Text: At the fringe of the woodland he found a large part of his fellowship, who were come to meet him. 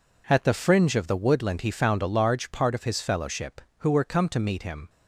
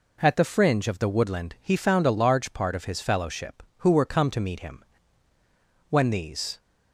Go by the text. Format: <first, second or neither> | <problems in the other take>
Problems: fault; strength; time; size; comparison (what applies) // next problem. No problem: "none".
first | goes on to say "When these"; noticeable; from 5.8 s on; 0.70 s long